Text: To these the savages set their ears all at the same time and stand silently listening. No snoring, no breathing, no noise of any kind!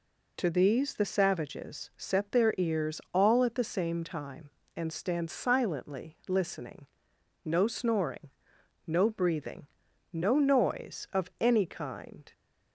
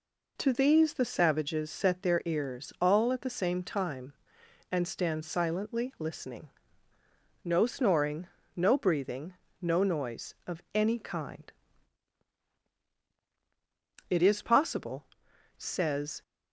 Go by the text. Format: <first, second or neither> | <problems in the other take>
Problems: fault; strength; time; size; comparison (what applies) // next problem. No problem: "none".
first | goes on to say "It is possible says"; strong; from 14.1 s on; 2.1 s long